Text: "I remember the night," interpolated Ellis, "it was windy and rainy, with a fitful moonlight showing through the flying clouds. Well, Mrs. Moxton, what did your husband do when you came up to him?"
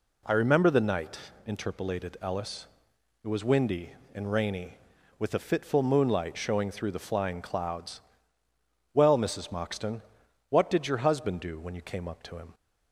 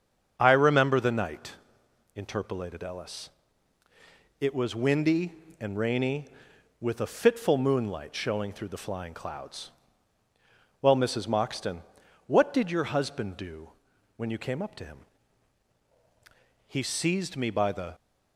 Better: first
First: none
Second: starts louder than the rest; until 1.3 s; 6.5 dB // pauses between "do" and "when"; noticeable; at 13.7 s; 0.46 s long // goes on to say "He seized me by the"; noticeable; from 16.6 s on; 1.2 s long

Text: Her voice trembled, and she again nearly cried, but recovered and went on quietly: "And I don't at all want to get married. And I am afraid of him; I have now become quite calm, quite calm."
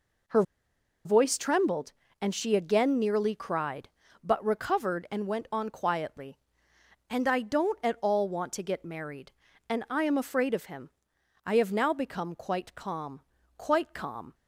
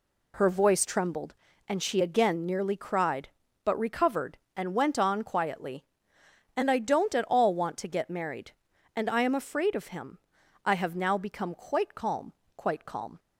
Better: second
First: pauses between "Her" and "voice"; noticeable; at 0.4 s; 0.63 s long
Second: none

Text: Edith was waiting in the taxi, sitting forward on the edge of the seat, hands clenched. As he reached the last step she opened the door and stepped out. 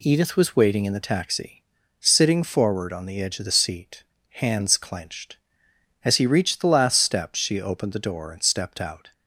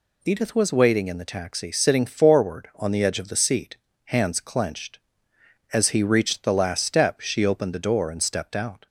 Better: neither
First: none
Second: none

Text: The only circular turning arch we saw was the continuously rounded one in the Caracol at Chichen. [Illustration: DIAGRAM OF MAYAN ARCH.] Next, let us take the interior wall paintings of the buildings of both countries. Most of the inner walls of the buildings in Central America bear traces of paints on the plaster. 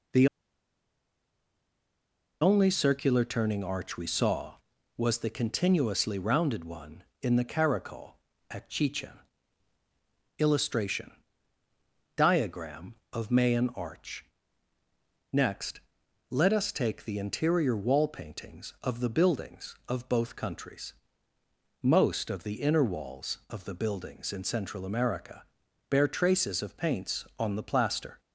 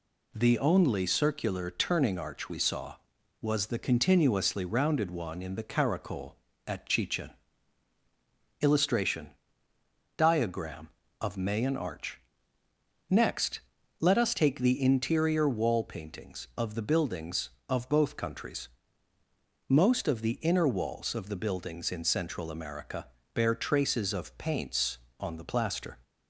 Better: second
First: pauses between "The" and "only"; strong; at 0.2 s; 2.1 s long // pauses between "America" and "bear"; noticeable; at 25.4 s; 0.48 s long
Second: pauses between "America" and "bear"; slight; at 23.0 s; 0.28 s long

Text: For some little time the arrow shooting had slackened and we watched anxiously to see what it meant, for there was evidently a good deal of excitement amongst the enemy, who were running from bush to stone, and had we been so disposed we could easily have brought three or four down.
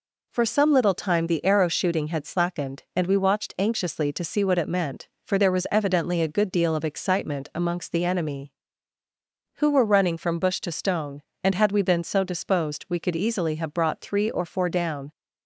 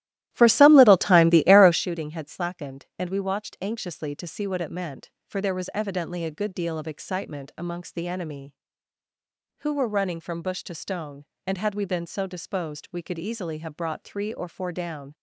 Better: first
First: none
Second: starts louder than the rest; strong; until 1.8 s; 14.5 dB

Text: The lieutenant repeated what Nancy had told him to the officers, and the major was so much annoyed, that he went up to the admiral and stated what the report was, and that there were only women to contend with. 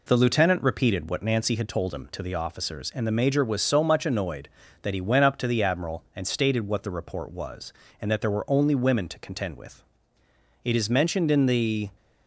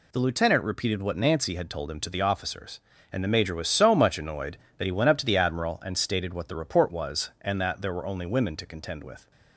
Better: second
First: goes on to say "It is mentioned in the"; noticeable; from 10.6 s on; 1.2 s long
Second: none

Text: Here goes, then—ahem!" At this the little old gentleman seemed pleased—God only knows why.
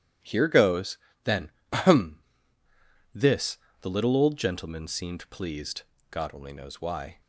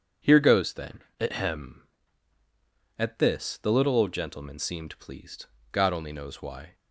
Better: second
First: starts louder than the rest; strong; until 1.4 s; 11 dB // skips "At"; at 2.6 s // pauses between "this" and "the"; slight; at 3.5 s; 0.22 s long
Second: none

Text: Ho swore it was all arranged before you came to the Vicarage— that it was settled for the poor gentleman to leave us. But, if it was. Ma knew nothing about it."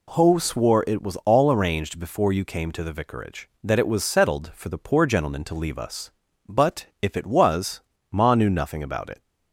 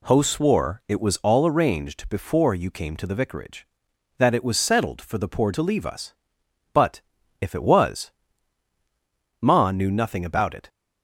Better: first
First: none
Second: skips "gentleman"; at 5.5 s

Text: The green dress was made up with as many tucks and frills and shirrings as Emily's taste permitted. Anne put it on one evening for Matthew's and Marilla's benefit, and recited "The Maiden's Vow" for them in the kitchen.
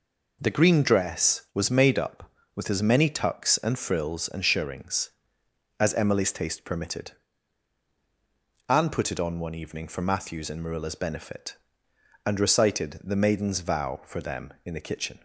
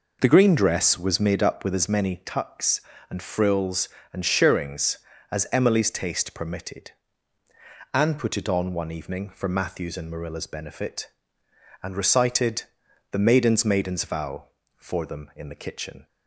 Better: first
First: none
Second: pauses between "recited" and "The"; noticeable; at 12.6 s; 0.48 s long // says "Maiden's" twice; at 13.6 s

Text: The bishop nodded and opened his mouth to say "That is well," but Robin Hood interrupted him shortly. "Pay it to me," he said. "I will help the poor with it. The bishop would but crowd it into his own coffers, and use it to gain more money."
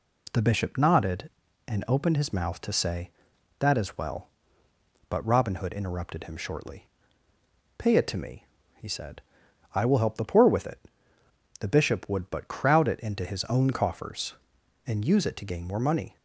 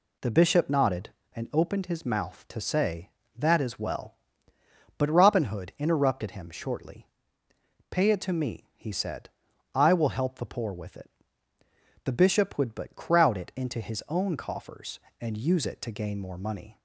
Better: neither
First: none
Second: none

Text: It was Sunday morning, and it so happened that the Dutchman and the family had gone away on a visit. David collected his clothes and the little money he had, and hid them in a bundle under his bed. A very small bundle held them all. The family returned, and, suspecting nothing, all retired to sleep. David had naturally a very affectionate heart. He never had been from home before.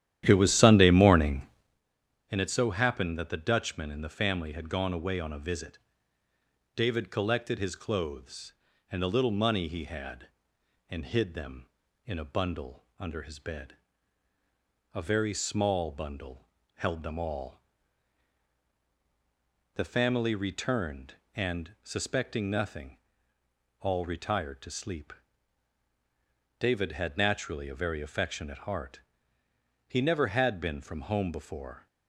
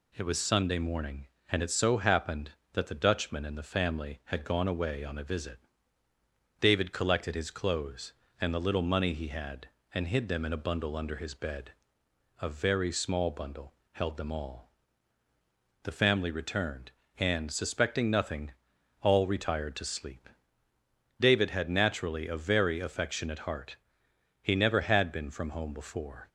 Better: second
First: starts louder than the rest; strong; until 1.8 s; 11.5 dB // pauses between "bundle" and "held"; slight; at 16.4 s; 0.30 s long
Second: pauses between "bundle" and "held"; slight; at 13.7 s; 0.20 s long

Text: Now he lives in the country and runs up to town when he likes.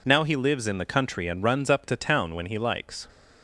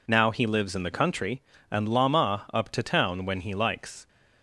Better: first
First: none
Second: says "lama" for "runs"; at 1.8 s

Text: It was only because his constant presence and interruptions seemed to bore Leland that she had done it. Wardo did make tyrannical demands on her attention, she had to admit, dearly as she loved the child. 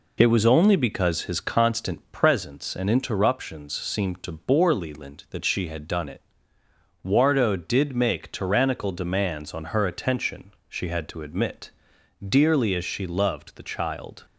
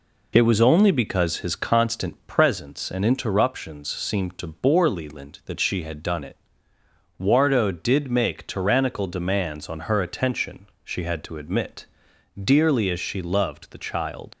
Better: first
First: none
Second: leaves "child" unfinished; at 14.3 s; 70 ms

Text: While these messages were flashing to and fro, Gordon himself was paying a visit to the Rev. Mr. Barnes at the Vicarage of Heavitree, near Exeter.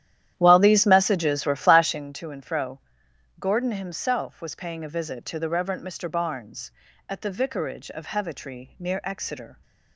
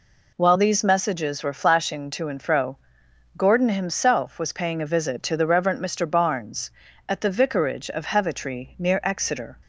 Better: second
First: starts louder than the rest; strong; until 2.2 s; 11.5 dB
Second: none

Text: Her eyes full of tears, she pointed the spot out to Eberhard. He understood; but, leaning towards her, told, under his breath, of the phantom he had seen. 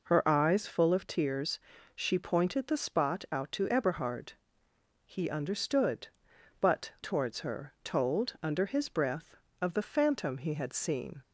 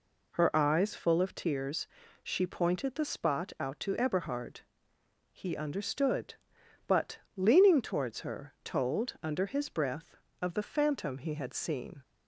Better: second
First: skips "leaning"; at 6.9 s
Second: none

